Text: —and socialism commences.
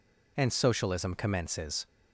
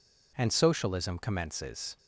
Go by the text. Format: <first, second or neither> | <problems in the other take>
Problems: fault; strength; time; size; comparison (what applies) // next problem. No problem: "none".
neither | none